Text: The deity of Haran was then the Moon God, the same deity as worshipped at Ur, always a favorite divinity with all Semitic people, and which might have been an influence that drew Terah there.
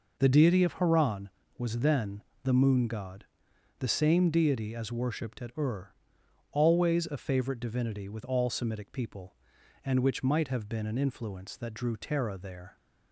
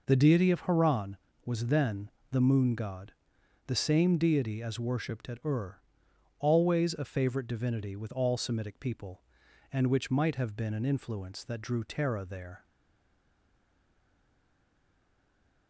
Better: first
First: pauses between "then" and "the"; slight; at 2.2 s; 0.20 s long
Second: pauses between "then" and "the"; slight; at 2.1 s; 0.20 s long // stays silent after the last word; strong; from 12.6 s on; 3.0 s long

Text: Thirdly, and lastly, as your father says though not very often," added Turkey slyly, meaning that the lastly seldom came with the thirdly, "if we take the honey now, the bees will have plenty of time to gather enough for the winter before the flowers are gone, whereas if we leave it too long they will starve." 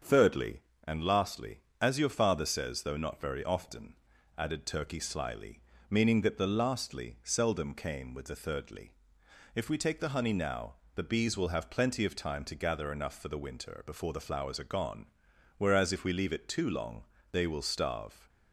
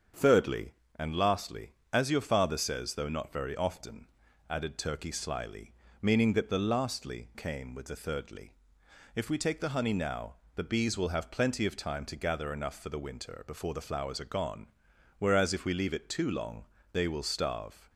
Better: first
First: starts louder than the rest; until 1.2 s; 7 dB // pauses between "long" and "they"; slight; at 17.0 s; 0.26 s long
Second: starts louder than the rest; strong; until 1.4 s; 7 dB // skips "seldom"; at 7.3 s // pauses between "long" and "they"; slight; at 16.6 s; 0.26 s long

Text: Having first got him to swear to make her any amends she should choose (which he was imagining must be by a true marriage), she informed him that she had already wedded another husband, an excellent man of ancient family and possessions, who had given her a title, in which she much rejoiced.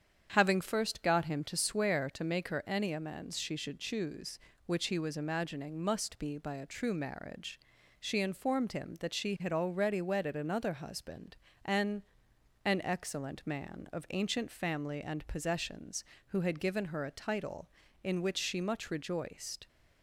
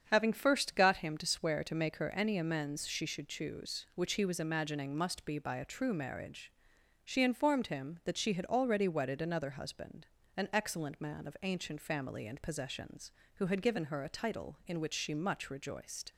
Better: second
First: starts louder than the rest; strong; until 1.3 s; 8 dB // says "an" twice; at 12.6 s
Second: starts louder than the rest; strong; until 1.1 s; 7.5 dB

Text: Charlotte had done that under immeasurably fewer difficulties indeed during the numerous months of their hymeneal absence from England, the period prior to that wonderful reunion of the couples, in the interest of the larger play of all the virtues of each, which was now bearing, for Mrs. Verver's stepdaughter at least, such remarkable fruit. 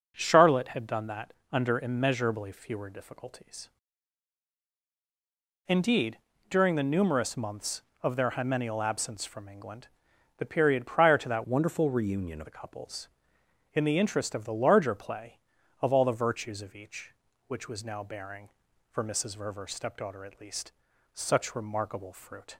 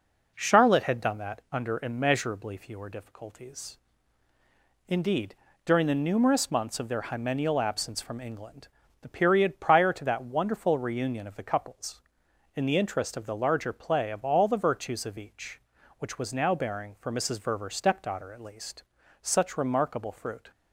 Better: second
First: pauses between "that" and "under"; slight; at 1.3 s; 0.18 s long // pauses between "difficulties" and "indeed"; strong; at 3.6 s; 2.0 s long // pauses between "indeed" and "during"; slight; at 6.1 s; 0.32 s long // changes voice from "wonderful" to "of"; from 11.4 to 12.4 s; 1.0 s long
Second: pauses between "difficulties" and "indeed"; at 3.7 s; 1.1 s long // pauses between "indeed" and "during"; slight; at 5.3 s; 0.30 s long

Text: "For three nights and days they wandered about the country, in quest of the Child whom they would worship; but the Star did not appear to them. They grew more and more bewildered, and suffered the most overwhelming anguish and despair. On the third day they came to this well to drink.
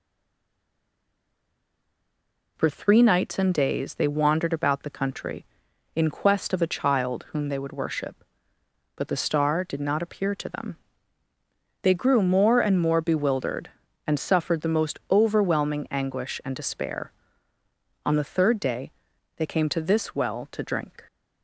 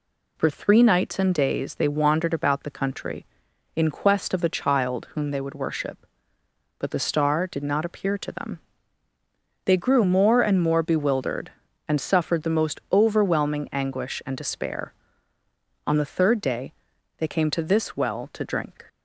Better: second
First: stays silent before the first word; strong; until 2.5 s; 2.5 s long // pauses between "day" and "they"; at 18.9 s; 0.42 s long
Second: pauses between "day" and "they"; at 16.7 s; 0.42 s long

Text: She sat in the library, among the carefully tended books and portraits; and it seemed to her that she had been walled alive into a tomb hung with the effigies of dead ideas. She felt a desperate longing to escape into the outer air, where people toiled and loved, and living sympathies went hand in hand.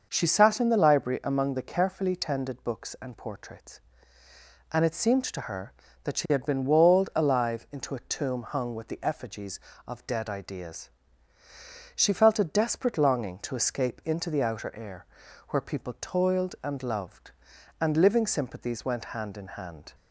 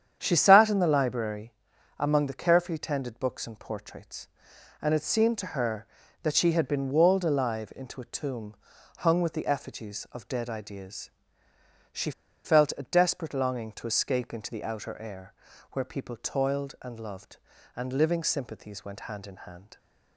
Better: first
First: starts louder than the rest; until 1.1 s; 6 dB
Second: starts louder than the rest; strong; until 1.2 s; 8.5 dB // pauses between "tomb" and "hung"; at 8.5 s; 0.44 s long // pauses between "She" and "felt"; slight; at 12.1 s; 0.33 s long

